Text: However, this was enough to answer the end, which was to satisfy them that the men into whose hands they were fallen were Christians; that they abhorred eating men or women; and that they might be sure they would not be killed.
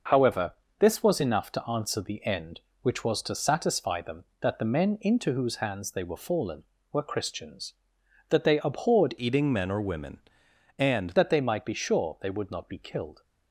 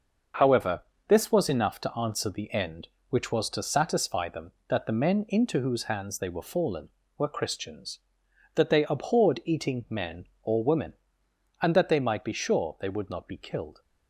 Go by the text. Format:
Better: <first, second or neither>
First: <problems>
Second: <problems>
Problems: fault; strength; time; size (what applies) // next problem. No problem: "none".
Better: second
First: changes voice from "eating" to "and"; from 9.1 to 11.0 s; 1.9 s long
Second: none